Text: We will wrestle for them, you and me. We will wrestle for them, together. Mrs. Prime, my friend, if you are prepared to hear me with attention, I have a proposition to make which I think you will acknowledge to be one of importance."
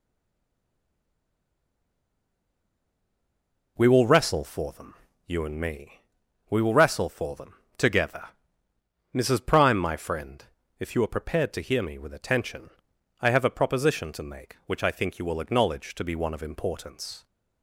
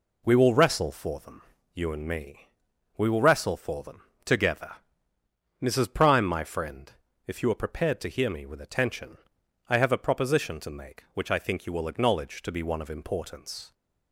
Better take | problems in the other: second | stays silent before the first word; strong; until 3.7 s; 3.7 s long

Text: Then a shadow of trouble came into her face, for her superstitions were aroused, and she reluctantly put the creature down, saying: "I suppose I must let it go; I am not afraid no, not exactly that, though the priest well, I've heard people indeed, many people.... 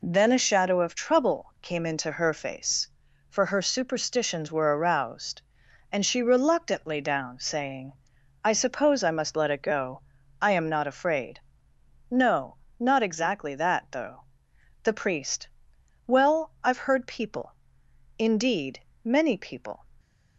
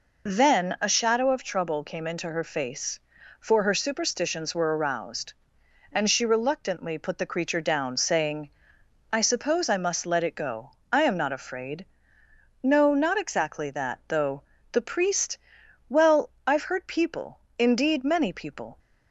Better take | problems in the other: second | skips "put the creature"; at 6.9 s // pauses between "afraid" and "no"; noticeable; at 11.3 s; 0.72 s long; noticeable in the second // pauses between "though" and "the"; noticeable; at 14.2 s; 0.58 s long; slight in the second // pauses between "priest" and "well"; noticeable; at 15.4 s; 0.62 s long; noticeable in the second // pauses between "people" and "indeed"; noticeable; at 17.5 s; 0.66 s long; slight in the second

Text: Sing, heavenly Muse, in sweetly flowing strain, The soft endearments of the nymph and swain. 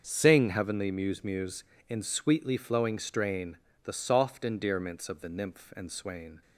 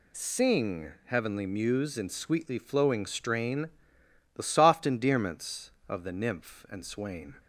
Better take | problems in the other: second | starts louder than the rest; until 1.0 s; 6.5 dB // says "Muse" twice; at 1.2 s

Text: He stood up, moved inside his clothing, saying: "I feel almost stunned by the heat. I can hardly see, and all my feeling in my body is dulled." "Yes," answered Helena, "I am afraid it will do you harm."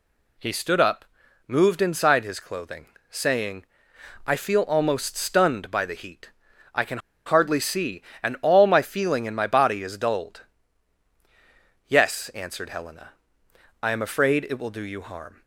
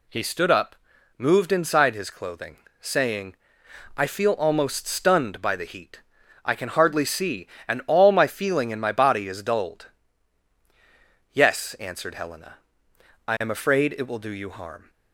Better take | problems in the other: second | pauses between "can" and "hardly"; slight; at 6.9 s; 0.28 s long

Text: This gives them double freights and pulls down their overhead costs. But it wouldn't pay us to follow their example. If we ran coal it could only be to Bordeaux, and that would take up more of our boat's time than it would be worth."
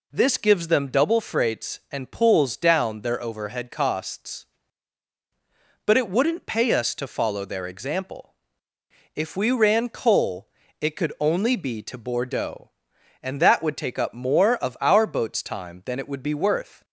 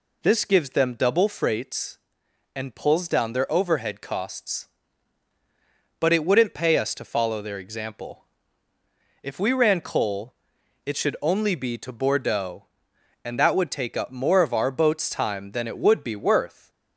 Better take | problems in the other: first | pauses between "coal" and "it"; noticeable; at 10.3 s; 0.50 s long; slight in the first // says "should" for "could"; at 10.9 s

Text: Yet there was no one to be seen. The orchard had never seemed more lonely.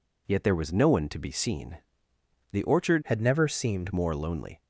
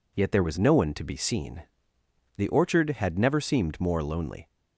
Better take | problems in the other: second | changes voice from "had" to "seemed"; from 3.0 to 3.9 s; 0.9 s long

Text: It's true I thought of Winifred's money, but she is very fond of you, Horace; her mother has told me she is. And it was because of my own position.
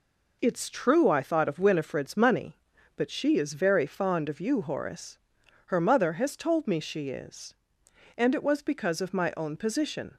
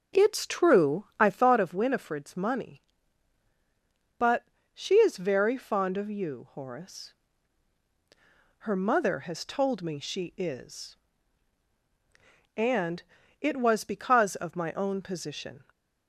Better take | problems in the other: first | starts louder than the rest; noticeable; until 1.4 s; 6 dB // pauses between "but" and "she"; slight; at 4.4 s; 0.28 s long // pauses between "And" and "it"; at 13.0 s; 0.40 s long

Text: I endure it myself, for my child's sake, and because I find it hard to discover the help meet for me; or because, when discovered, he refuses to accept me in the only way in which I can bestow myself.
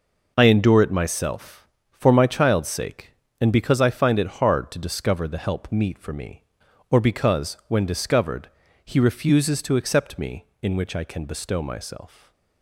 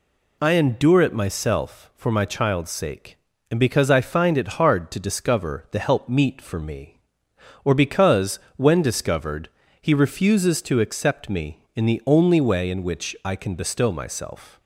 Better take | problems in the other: second | skips "in the only way"; at 10.5 s // stays silent after the last word; slight; from 12.0 s on; 0.6 s long

